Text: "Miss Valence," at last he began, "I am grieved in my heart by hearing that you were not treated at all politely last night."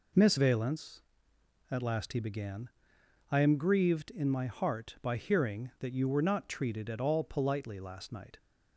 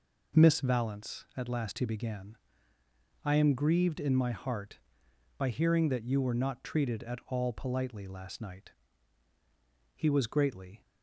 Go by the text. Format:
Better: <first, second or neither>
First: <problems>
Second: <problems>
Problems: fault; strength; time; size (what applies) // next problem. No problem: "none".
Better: first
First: none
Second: goes on to say "He was greatly"; noticeable; from 9.9 s on; 0.88 s long